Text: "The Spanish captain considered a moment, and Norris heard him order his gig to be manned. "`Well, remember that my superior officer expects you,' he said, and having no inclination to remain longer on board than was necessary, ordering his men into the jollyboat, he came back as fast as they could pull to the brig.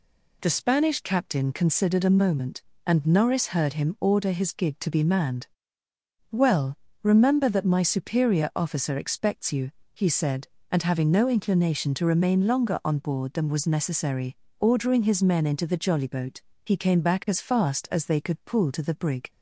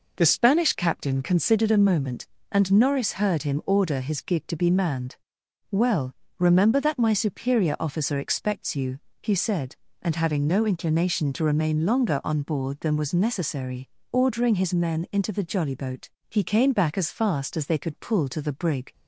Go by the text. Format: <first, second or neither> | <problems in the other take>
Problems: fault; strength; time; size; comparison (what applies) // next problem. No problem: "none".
neither | none